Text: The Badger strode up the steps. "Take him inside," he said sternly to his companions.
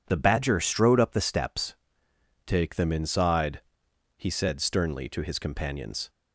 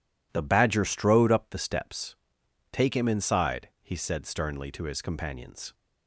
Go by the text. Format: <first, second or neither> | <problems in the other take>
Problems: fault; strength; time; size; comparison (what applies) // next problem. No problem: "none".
second | says "them" for "him"; at 2.7 s